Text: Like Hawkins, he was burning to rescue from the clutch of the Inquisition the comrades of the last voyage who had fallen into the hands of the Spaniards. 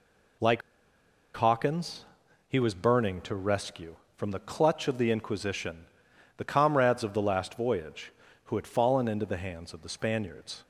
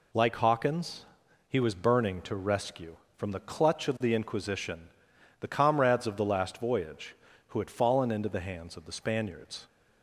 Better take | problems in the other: second | pauses between "Like" and "Hawkins"; noticeable; at 0.6 s; 0.75 s long // pauses between "Inquisition" and "the"; noticeable; at 5.8 s; 0.52 s long; noticeable in the second

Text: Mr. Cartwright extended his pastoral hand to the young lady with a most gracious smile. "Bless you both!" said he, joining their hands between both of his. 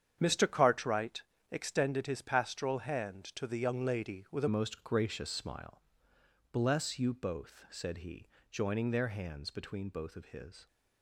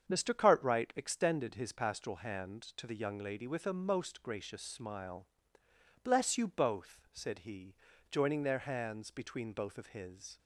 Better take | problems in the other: second | starts louder than the rest; strong; until 1.2 s; 8.5 dB; strong in the second // pauses between "Cartwright" and "extended"; slight; at 1.2 s; 0.28 s long // changes voice at "most"; from 4.4 s on; 6.2 s long

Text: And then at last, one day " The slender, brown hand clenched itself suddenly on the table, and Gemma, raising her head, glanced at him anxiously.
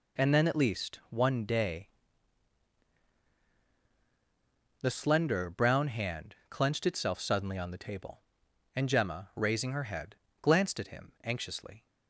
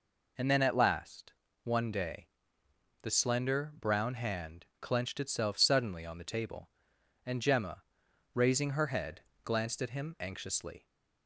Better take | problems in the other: second | says "least" for "last"; at 0.5 s

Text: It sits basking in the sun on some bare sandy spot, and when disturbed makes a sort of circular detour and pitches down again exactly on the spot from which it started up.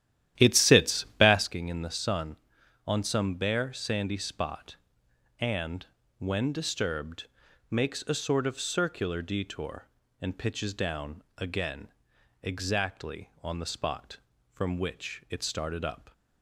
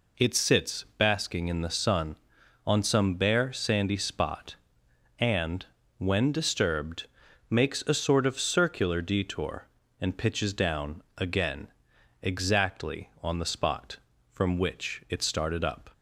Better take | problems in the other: second | starts louder than the rest; strong; until 1.6 s; 12 dB // pauses between "and" and "when"; slight; at 5.8 s; 0.32 s long; slight in the second // pauses between "disturbed" and "makes"; at 7.2 s; 0.42 s long; also in the second // pauses between "again" and "exactly"; noticeable; at 11.8 s; 0.56 s long; noticeable in the second

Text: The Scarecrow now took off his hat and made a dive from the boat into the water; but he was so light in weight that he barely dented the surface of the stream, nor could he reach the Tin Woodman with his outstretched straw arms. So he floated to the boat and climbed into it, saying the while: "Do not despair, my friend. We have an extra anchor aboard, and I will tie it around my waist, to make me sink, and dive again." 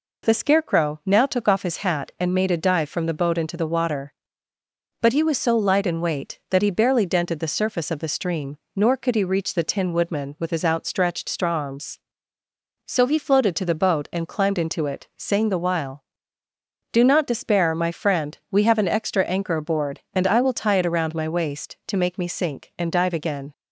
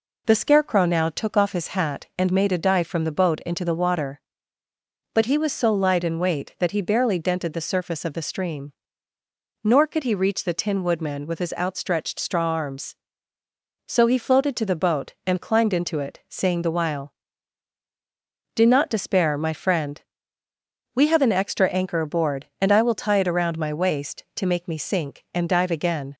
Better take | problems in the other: neither | none

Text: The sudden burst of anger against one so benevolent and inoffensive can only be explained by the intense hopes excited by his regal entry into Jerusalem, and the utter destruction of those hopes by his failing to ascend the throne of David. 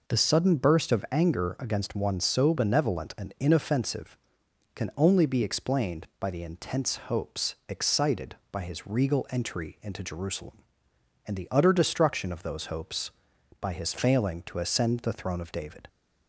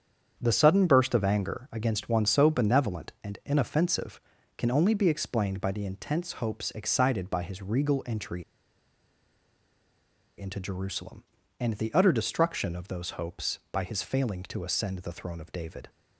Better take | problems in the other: first | starts louder than the rest; strong; until 1.4 s; 8 dB // pauses between "entry" and "into"; strong; at 8.4 s; 1.9 s long

